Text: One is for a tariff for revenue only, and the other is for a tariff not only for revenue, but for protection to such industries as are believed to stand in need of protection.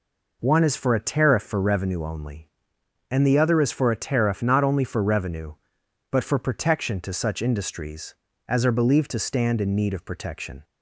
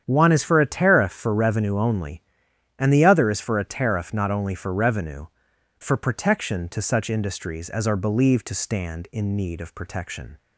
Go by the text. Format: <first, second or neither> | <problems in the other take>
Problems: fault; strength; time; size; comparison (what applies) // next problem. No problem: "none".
first | starts louder than the rest; strong; until 1.0 s; 9 dB // skips "but"; at 5.5 s